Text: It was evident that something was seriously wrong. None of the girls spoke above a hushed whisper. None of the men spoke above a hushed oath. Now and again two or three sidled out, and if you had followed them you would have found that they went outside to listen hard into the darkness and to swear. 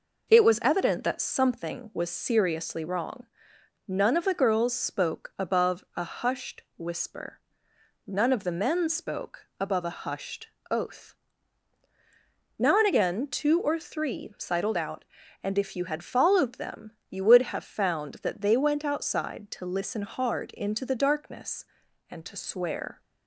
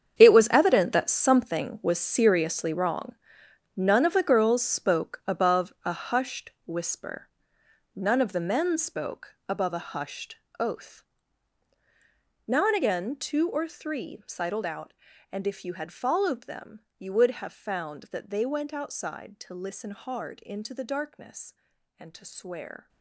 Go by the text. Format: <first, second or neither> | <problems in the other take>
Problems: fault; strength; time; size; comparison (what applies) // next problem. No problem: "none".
first | gets quieter; strong; throughout; 14 dB // pauses between "hushed" and "oath"; slight; at 10.3 s; 0.22 s long; slight in the first // pauses between "them" and "you"; slight; at 16.8 s; 0.18 s long; slight in the first